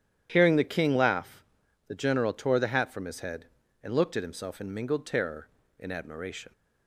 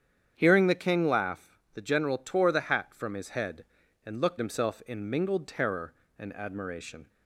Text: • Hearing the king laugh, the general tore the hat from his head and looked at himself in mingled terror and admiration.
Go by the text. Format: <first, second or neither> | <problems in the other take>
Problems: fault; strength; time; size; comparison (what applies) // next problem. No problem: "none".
first | starts louder than the rest; strong; until 1.3 s; 8.5 dB; strong in the first // skips "at"; at 4.3 s